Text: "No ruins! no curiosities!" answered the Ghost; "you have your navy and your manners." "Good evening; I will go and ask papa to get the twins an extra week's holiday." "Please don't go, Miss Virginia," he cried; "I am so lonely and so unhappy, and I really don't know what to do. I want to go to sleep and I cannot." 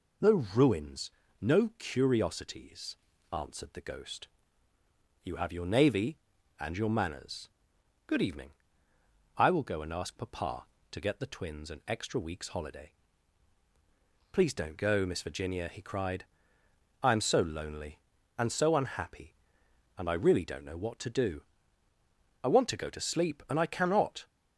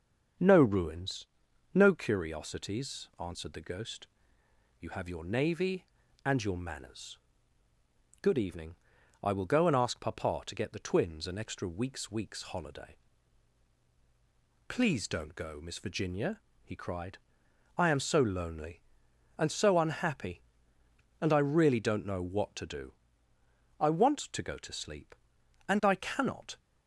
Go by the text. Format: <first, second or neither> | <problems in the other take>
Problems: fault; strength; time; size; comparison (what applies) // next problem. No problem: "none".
first | starts louder than the rest; strong; until 1.8 s; 7 dB // says "week's" twice; at 12.1 s